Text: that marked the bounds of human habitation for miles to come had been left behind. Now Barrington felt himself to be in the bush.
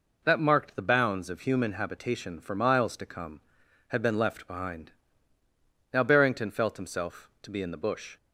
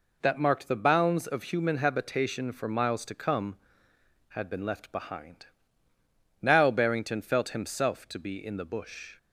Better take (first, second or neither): neither